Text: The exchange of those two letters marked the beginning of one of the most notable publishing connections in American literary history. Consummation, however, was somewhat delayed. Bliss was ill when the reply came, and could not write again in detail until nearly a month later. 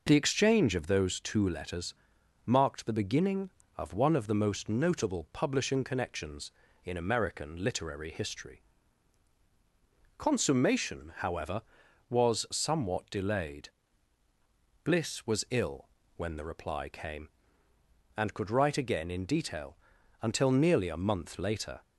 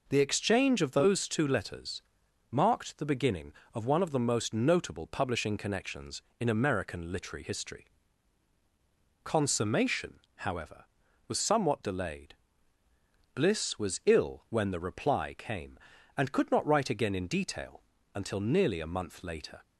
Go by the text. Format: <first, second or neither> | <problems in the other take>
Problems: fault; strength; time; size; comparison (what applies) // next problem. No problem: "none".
second | pauses between "letters" and "marked"; noticeable; at 1.9 s; 0.52 s long; noticeable in the second // pauses between "ill" and "when"; slight; at 15.8 s; 0.26 s long // skips "not"; at 18.4 s // pauses between "detail" and "until"; noticeable; at 19.7 s; 0.46 s long; slight in the second